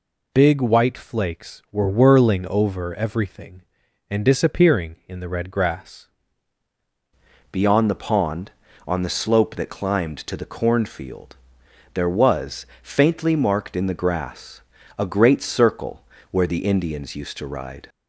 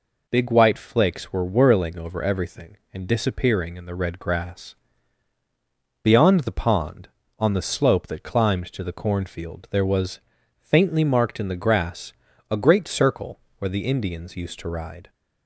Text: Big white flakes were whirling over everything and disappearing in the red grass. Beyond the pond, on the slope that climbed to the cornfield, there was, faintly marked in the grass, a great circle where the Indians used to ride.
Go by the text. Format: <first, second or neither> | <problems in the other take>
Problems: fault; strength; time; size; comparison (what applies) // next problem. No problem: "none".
second | changes voice at "Beyond"; from 7.5 s on; 10.3 s long // pauses between "circle" and "where"; slight; at 16.0 s; 0.28 s long; slight in the second